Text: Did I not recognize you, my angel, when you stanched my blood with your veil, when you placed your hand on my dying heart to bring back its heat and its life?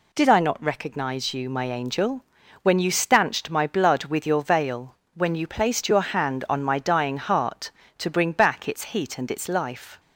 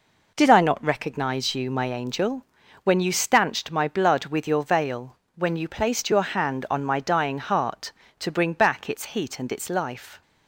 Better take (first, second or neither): first